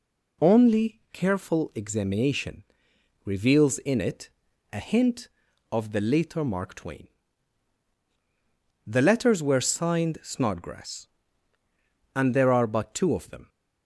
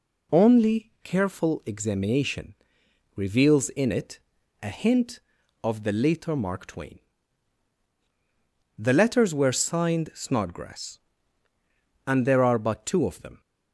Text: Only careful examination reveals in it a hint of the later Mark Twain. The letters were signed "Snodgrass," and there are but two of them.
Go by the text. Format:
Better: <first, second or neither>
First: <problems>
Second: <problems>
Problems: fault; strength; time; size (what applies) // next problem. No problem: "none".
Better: neither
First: pauses between "examination" and "reveals"; noticeable; at 2.6 s; 0.62 s long // pauses between "it" and "a"; at 4.3 s; 0.42 s long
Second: pauses between "examination" and "reveals"; noticeable; at 2.5 s; 0.62 s long // pauses between "it" and "a"; at 4.2 s; 0.42 s long